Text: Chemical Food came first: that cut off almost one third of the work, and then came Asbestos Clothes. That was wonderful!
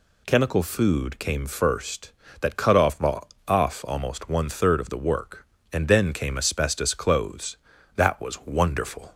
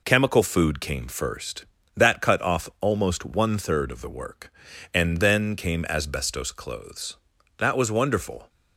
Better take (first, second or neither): second